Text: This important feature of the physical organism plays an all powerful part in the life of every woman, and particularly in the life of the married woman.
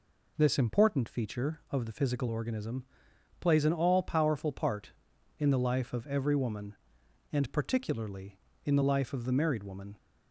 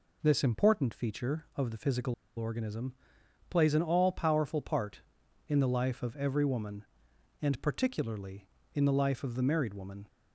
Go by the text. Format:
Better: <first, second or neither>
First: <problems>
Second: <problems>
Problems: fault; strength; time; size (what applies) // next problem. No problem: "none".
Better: first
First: pauses between "organism" and "plays"; noticeable; at 2.8 s; 0.54 s long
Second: pauses between "physical" and "organism"; slight; at 2.1 s; 0.22 s long // pauses between "organism" and "plays"; noticeable; at 2.9 s; 0.54 s long